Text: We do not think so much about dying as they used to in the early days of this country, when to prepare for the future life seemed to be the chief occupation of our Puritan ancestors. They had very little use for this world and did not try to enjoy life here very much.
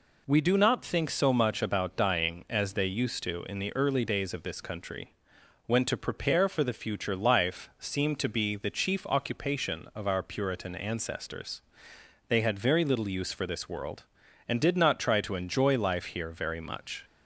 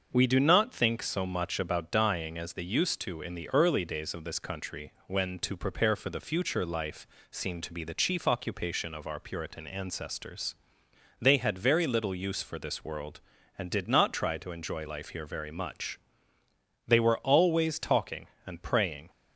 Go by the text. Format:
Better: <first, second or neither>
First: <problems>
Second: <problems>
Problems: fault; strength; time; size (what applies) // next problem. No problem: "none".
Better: first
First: none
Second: starts louder than the rest; until 1.1 s; 6.5 dB // pauses between "life" and "seemed"; slight; at 7.0 s; 0.24 s long // goes on to say "They were always talking and praying"; strong; from 16.8 s on; 2.2 s long